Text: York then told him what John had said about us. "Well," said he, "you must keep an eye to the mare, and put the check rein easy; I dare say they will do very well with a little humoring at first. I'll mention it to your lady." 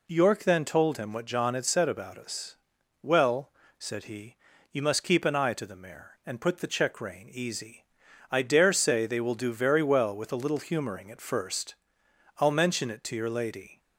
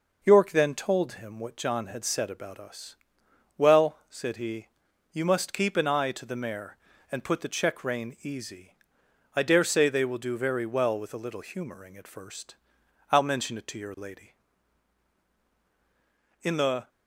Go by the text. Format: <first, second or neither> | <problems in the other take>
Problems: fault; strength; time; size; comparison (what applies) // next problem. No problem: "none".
first | goes on to say "In the"; slight; from 16.4 s on; 0.46 s long